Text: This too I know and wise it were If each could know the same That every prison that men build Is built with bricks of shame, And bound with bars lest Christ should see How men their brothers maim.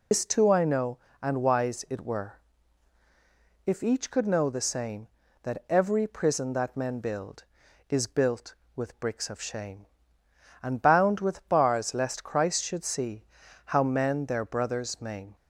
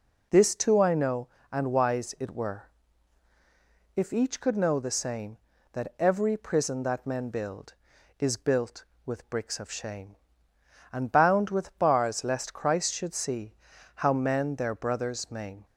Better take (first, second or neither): second